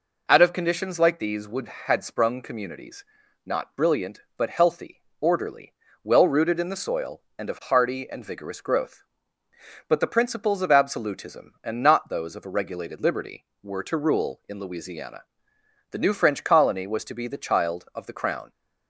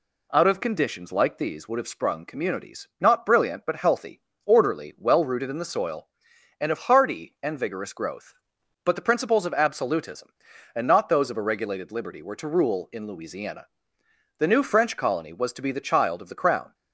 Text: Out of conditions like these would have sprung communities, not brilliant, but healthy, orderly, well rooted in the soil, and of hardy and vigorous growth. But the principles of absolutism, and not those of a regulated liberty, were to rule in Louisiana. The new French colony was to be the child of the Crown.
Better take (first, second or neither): second